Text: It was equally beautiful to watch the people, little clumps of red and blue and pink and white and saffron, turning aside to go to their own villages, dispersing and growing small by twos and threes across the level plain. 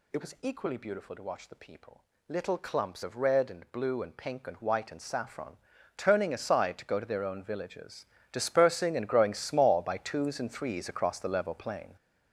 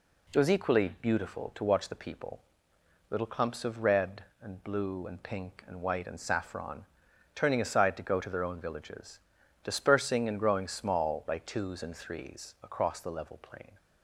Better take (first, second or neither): second